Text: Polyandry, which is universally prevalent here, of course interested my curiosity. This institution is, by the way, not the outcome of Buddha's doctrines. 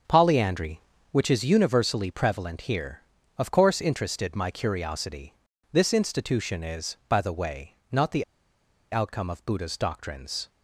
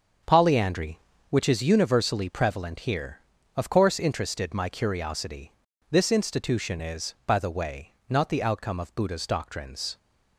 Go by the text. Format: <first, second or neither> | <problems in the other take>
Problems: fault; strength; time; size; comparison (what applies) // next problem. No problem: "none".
second | starts louder than the rest; until 1.3 s; 7 dB; also in the second // pauses between "the" and "outcome"; noticeable; at 8.2 s; 0.68 s long